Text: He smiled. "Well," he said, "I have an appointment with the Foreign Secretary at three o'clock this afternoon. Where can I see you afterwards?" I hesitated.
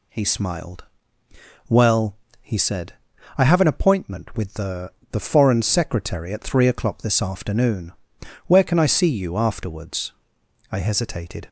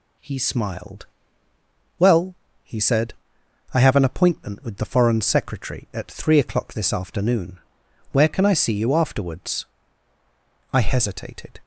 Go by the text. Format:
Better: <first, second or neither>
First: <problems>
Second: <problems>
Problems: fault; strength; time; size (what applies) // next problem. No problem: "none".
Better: second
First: says "the" twice; at 5.1 s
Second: none